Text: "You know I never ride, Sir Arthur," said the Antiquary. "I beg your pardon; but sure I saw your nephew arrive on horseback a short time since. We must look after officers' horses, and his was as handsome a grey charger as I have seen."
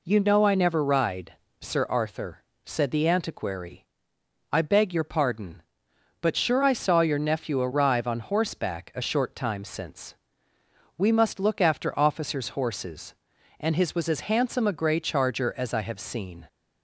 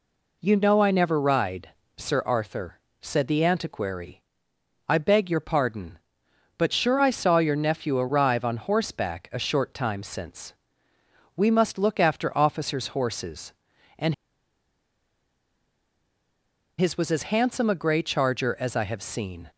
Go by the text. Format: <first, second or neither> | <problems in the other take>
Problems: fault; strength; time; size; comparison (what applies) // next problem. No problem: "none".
first | pauses between "and" and "his"; strong; at 14.1 s; 2.6 s long